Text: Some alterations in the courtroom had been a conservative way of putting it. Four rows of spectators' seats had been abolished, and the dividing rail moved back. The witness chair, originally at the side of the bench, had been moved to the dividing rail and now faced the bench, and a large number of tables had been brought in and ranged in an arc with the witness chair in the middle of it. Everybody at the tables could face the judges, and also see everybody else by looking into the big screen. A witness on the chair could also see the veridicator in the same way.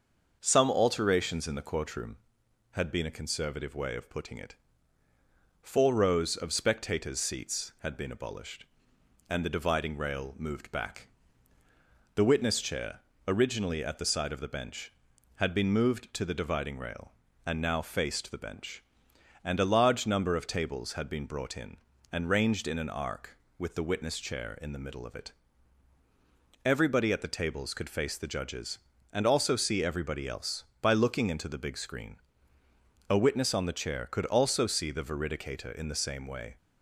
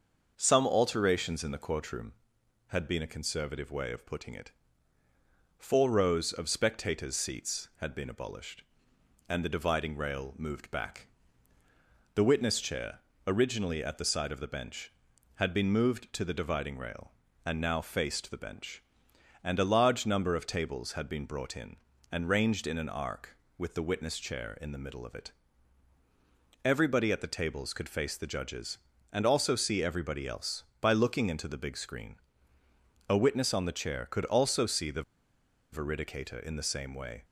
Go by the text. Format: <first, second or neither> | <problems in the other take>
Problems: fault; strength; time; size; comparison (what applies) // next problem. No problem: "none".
first | starts louder than the rest; until 1.3 s; 6.5 dB; also in the first // pauses between "the" and "veridicator"; noticeable; at 35.0 s; 0.69 s long